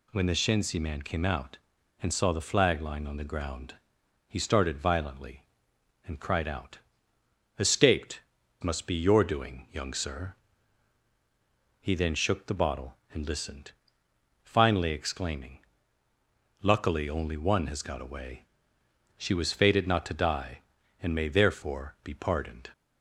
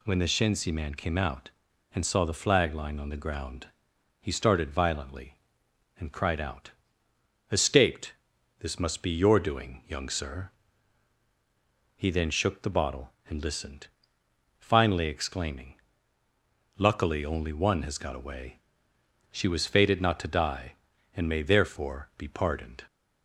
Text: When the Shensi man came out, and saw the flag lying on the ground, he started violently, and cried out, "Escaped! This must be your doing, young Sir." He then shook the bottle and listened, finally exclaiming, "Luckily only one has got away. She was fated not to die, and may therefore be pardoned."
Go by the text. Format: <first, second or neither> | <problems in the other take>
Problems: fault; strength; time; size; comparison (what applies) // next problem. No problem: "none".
second | skips "This"; at 8.4 s